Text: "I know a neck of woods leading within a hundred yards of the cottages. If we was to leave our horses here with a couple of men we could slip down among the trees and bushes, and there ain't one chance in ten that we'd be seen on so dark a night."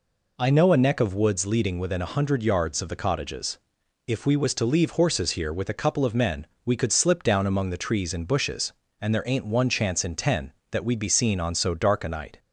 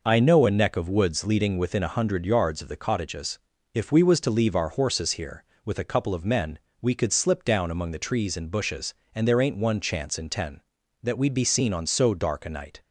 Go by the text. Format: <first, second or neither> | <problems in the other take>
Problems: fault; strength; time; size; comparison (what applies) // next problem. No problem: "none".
second | skips "our"; at 4.9 s // pauses between "men" and "we"; slight; at 6.4 s; 0.18 s long; slight in the second